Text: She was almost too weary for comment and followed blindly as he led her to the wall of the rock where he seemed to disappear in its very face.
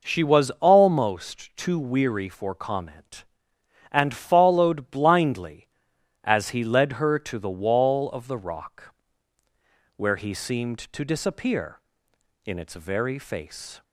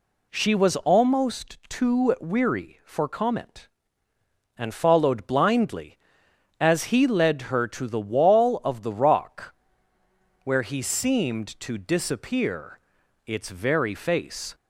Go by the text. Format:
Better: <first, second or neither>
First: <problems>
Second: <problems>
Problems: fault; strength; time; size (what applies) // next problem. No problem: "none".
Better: first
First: pauses between "rock" and "where"; at 8.9 s; 1.0 s long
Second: pauses between "rock" and "where"; noticeable; at 9.5 s; 0.92 s long // skips "in"; at 13.0 s